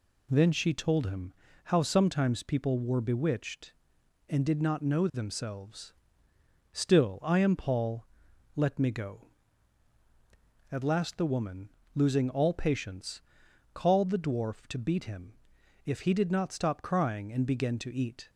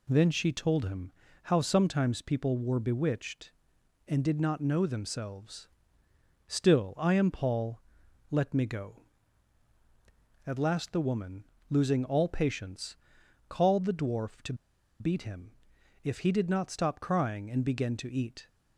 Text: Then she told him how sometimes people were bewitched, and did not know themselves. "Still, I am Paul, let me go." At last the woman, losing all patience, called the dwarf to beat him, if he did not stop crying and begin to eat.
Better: first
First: pauses between "him" and "how"; slight; at 1.3 s; 0.34 s long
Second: pauses between "him" and "how"; slight; at 1.1 s; 0.34 s long // pauses between "to" and "beat"; at 14.5 s; 0.45 s long

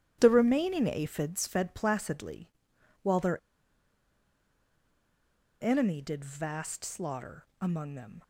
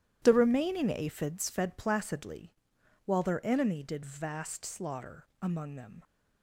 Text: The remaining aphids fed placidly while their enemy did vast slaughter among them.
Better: second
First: starts louder than the rest; strong; until 1.2 s; 12 dB // pauses between "placidly" and "while"; noticeable; at 2.4 s; 0.54 s long // pauses between "their" and "enemy"; strong; at 3.3 s; 2.2 s long // pauses between "slaughter" and "among"; slight; at 7.4 s; 0.16 s long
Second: starts louder than the rest; strong; until 1.2 s; 12 dB // pauses between "placidly" and "while"; noticeable; at 2.5 s; 0.54 s long // pauses between "slaughter" and "among"; slight; at 5.2 s; 0.16 s long

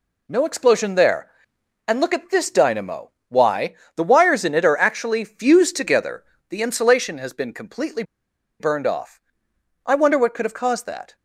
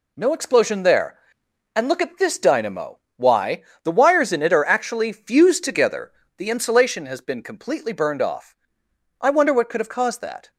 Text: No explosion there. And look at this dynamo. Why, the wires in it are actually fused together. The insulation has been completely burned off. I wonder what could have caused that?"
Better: second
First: pauses between "completely" and "burned"; noticeable; at 8.0 s; 0.57 s long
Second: none

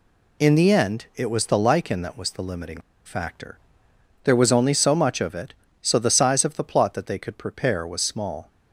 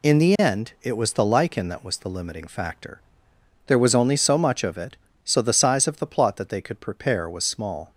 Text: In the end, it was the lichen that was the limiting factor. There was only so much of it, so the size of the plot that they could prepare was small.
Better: second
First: pauses between "limiting" and "factor"; slight; at 2.7 s; 0.25 s long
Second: none

